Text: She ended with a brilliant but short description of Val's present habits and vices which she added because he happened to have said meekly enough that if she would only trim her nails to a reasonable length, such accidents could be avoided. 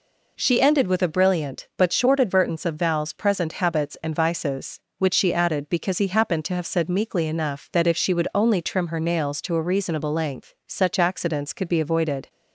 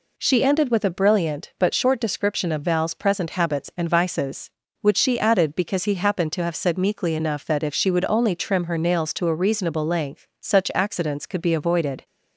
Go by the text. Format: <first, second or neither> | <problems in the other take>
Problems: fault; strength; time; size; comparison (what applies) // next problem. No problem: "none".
second | says "advertence" for "description"; at 2.1 s